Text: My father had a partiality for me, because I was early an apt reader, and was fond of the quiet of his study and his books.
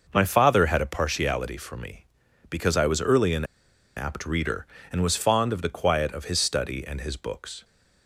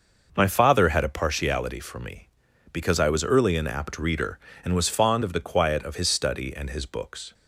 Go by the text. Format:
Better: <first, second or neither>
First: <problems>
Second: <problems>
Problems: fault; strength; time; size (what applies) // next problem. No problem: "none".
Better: second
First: starts louder than the rest; noticeable; until 1.1 s; 6 dB // pauses between "an" and "apt"; noticeable; at 3.4 s; 0.52 s long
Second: none